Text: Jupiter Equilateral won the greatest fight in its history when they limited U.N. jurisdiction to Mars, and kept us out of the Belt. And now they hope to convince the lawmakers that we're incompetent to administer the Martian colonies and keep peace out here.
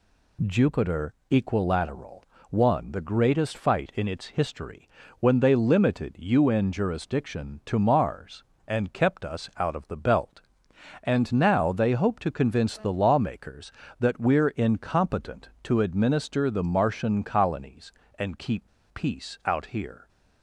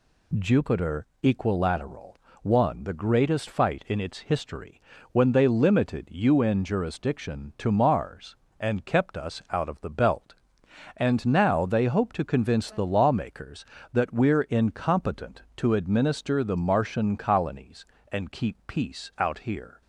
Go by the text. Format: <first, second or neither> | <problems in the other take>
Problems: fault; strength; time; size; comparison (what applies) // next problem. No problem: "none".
second | pauses between "Jupiter" and "Equilateral"; slight; at 1.1 s; 0.16 s long; slight in the second // pauses between "Equilateral" and "won"; slight; at 2.2 s; 0.26 s long; slight in the second // pauses between "history" and "when"; slight; at 4.8 s; 0.32 s long; slight in the second // pauses between "keep" and "peace"; slight; at 18.6 s; 0.28 s long